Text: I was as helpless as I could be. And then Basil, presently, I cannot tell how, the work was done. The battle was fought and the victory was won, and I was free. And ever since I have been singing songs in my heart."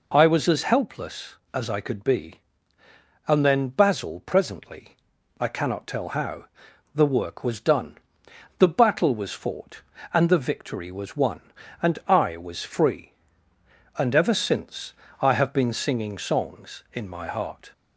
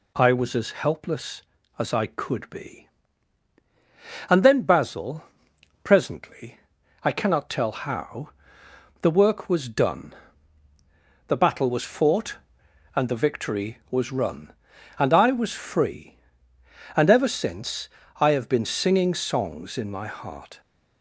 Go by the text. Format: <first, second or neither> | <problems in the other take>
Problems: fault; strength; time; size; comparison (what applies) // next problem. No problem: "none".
first | says "run" for "won"; at 14.1 s // pauses between "since" and "I"; slight; at 17.8 s; 0.30 s long; slight in the first